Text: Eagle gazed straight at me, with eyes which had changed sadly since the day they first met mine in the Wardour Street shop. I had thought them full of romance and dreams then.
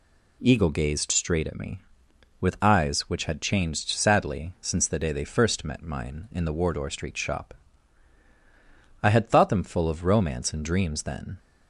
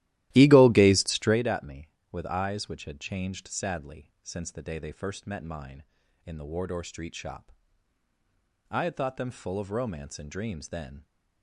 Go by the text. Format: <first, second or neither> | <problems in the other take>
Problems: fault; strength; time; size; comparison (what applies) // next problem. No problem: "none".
first | starts louder than the rest; strong; until 1.5 s; 15 dB